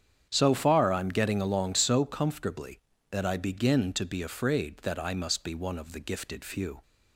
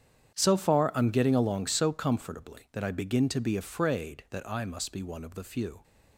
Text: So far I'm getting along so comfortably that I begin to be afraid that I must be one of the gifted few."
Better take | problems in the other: first | starts louder than the rest; strong; until 1.3 s; 9 dB; strong in the first // skips "gifted"; at 5.4 s

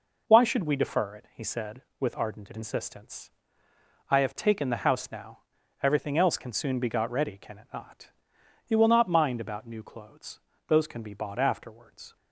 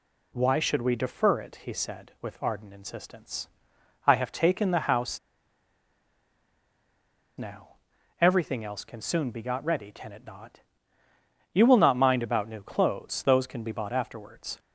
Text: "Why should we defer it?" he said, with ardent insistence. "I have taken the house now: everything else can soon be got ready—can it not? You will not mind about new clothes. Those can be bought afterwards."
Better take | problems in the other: first | pauses between "house" and "now"; strong; at 5.1 s; 2.1 s long

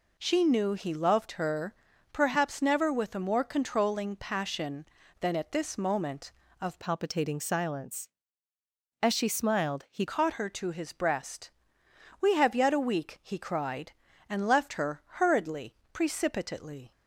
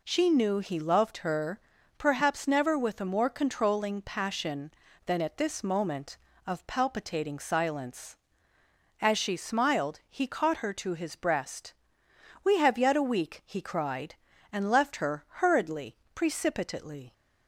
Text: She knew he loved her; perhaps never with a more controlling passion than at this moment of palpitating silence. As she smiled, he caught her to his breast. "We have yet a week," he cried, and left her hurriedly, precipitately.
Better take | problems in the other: second | changes voice from "palpitating" to "he"; from 6.7 to 10.0 s; 3.3 s long

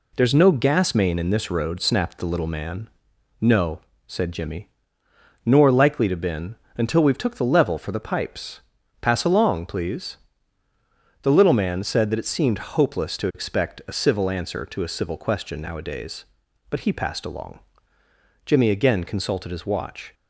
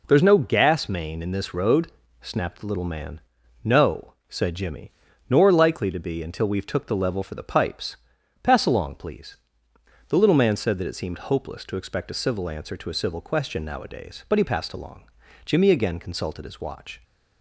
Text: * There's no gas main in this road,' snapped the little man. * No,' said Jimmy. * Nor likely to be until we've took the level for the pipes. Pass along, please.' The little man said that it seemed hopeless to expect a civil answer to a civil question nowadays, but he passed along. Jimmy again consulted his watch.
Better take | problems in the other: second | says "been" for "be"; at 6.1 s

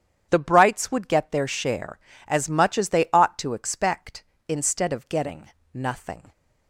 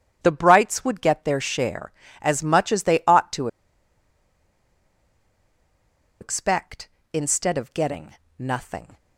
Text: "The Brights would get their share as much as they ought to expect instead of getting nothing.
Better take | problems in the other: first | starts louder than the rest; strong; until 1.2 s; 9 dB; strong in the first // pauses between "to" and "expect"; strong; at 3.4 s; 2.7 s long // pauses between "getting" and "nothing"; slight; at 8.1 s; 0.24 s long; slight in the first

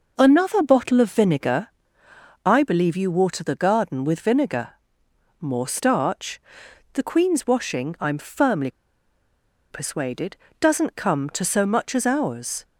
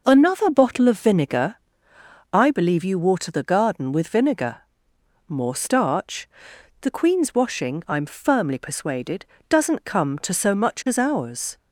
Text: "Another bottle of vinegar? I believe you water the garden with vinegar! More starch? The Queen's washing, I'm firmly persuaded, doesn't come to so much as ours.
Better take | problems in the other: second | pauses between "firmly" and "persuaded"; at 8.6 s; 1.0 s long

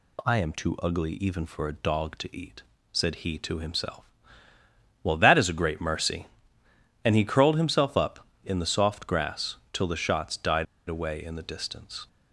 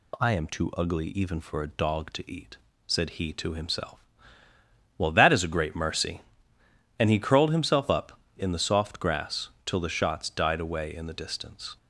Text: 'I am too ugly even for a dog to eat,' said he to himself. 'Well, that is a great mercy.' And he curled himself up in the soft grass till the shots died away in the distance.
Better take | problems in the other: second | pauses between "grass" and "till"; slight; at 9.5 s; 0.16 s long; slight in the second // pauses between "died" and "away"; slight; at 10.6 s; 0.24 s long

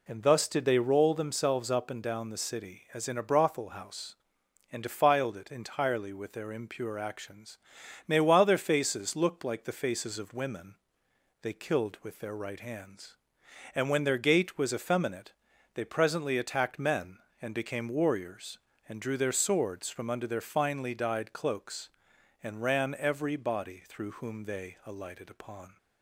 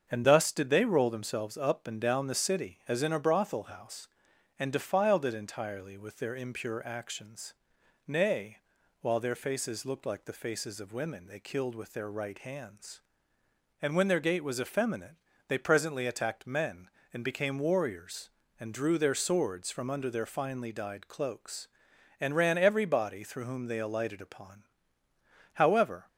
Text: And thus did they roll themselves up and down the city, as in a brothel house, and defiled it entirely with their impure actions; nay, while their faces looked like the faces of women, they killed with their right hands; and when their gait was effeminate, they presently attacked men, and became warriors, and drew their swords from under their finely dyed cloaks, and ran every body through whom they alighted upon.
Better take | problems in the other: first | starts louder than the rest; until 1.1 s; 7 dB // goes on to say "However"; from 25.5 s on; 0.52 s long

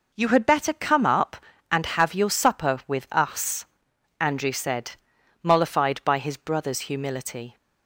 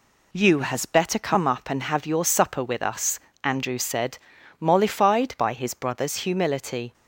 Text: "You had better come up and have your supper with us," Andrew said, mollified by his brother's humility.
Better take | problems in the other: first | says "has" for "had"; at 0.6 s

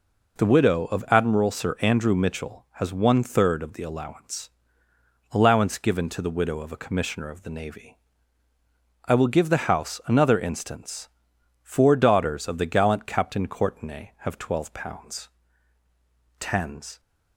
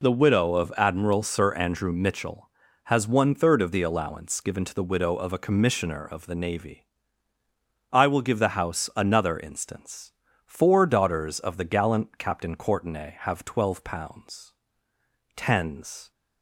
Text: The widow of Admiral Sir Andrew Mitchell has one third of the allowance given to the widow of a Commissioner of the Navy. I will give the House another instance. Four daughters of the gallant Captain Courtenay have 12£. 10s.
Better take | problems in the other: second | says "allowance" twice; at 5.3 s

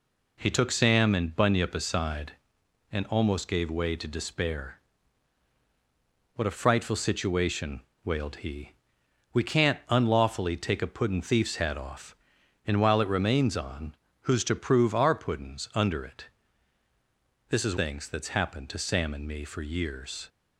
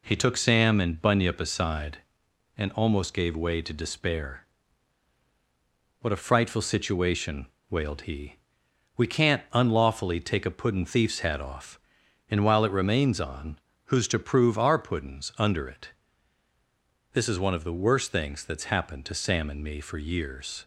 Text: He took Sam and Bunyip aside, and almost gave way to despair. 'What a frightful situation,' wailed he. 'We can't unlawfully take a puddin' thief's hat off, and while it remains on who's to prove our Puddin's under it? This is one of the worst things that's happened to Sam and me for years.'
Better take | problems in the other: second | pauses between "on" and "who's"; slight; at 13.9 s; 0.24 s long; slight in the second // skips "one of the worst"; at 17.7 s

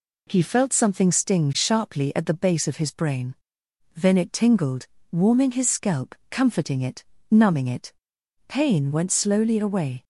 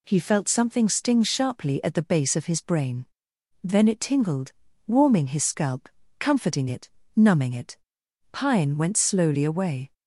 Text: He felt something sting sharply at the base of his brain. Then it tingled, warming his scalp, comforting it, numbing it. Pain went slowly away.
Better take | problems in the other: first | says "Pine" for "Pain"; at 8.3 s

